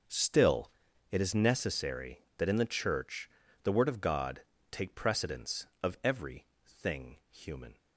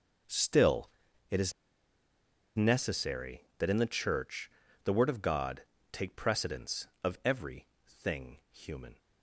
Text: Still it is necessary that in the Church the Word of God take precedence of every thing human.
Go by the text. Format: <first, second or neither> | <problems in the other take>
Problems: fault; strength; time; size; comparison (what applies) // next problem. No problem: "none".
first | starts louder than the rest; until 2.7 s; 6.5 dB; also in the first // pauses between "Still" and "it"; at 0.8 s; 0.42 s long; also in the first // pauses between "is" and "necessary"; at 1.5 s; 1.0 s long // pauses between "Church" and "the"; slight; at 4.5 s; 0.34 s long; slight in the first // pauses between "God" and "take"; slight; at 5.6 s; 0.30 s long; slight in the first // pauses between "every" and "thing"; slight; at 7.6 s; 0.18 s long; slight in the first